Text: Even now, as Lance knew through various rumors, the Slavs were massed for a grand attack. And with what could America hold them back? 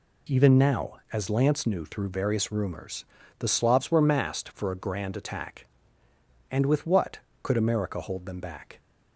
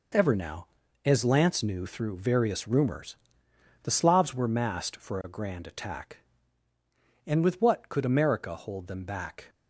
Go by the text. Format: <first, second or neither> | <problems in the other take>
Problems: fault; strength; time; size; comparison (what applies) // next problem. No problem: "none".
first | says "Ever" for "Even"; at 0.1 s